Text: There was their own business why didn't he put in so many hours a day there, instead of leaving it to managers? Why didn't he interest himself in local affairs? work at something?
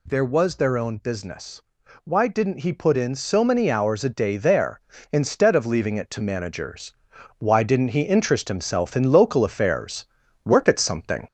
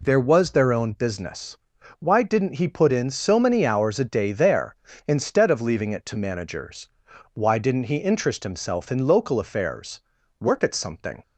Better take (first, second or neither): second